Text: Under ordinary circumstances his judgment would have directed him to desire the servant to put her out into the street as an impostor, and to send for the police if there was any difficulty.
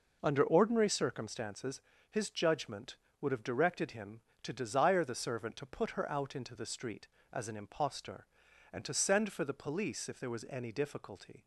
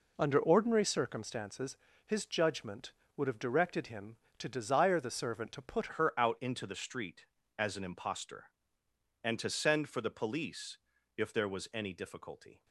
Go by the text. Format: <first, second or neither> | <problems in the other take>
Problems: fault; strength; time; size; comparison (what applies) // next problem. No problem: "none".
first | pauses between "circumstances" and "his"; slight; at 1.7 s; 0.28 s long; slight in the first // changes voice at "her"; from 5.9 s on; 6.7 s long // pauses between "police" and "if"; at 10.7 s; 0.38 s long